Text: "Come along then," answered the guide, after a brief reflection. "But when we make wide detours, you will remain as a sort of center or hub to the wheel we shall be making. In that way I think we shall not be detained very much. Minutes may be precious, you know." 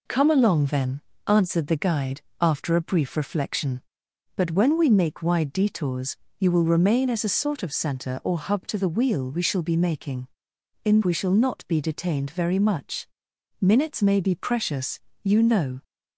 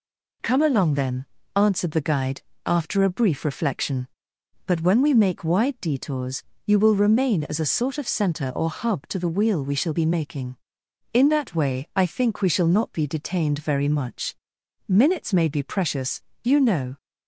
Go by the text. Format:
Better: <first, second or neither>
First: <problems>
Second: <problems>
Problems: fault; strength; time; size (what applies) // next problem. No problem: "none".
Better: second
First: skips "that way I think"; at 11.0 s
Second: none